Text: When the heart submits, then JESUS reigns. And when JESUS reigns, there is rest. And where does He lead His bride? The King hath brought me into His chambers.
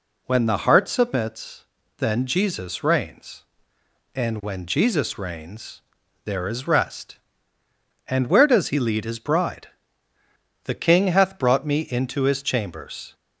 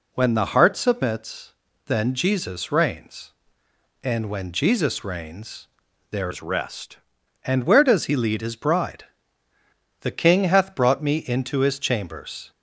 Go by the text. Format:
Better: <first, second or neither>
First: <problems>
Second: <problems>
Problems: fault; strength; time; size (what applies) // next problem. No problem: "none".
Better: first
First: none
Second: changes voice from "is" to "rest"; from 6.3 to 6.9 s; 0.6 s long